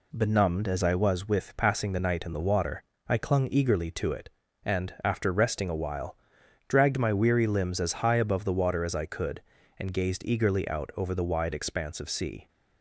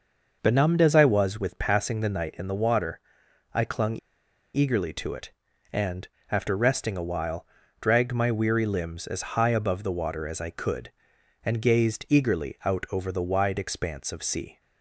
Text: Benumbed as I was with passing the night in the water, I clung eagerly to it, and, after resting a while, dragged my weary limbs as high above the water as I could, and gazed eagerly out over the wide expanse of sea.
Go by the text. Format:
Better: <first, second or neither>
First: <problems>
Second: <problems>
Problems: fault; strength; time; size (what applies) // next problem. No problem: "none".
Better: first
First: none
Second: pauses between "clung" and "eagerly"; noticeable; at 3.9 s; 0.56 s long